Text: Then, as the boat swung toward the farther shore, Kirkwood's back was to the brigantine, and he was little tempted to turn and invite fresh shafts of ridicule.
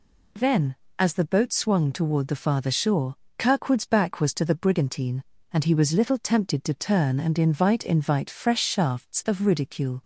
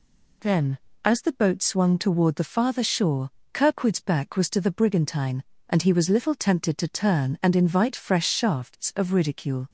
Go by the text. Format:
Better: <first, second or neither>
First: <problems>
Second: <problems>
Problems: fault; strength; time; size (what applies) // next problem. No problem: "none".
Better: second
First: says "invite" twice; at 7.8 s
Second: none